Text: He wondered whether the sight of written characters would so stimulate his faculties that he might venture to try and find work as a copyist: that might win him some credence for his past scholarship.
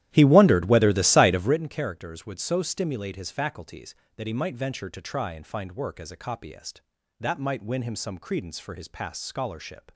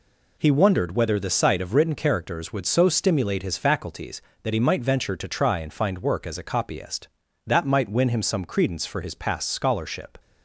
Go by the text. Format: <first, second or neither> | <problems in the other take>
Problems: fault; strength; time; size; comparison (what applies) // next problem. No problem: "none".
second | starts louder than the rest; strong; until 1.6 s; 13 dB